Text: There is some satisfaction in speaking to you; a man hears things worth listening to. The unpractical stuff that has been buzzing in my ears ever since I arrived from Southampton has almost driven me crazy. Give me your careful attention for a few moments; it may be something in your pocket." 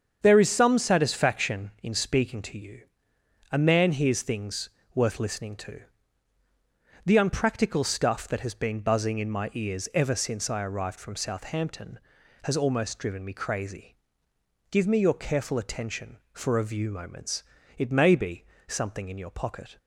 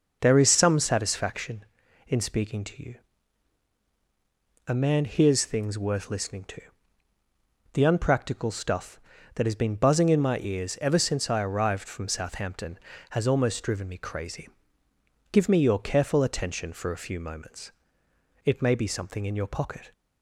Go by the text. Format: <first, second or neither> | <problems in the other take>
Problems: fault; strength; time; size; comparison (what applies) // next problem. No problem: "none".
second | starts louder than the rest; strong; until 1.2 s; 7 dB // pauses between "things" and "worth"; slight; at 4.6 s; 0.28 s long // says "view" for "few"; at 16.6 s // pauses between "be" and "something"; slight; at 18.4 s; 0.22 s long